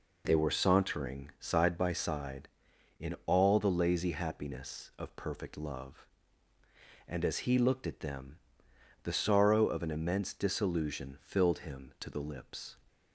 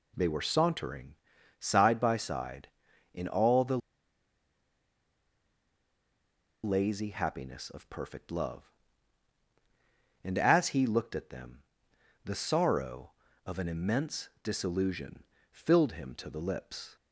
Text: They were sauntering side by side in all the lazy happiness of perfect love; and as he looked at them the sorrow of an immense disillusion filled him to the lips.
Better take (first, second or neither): first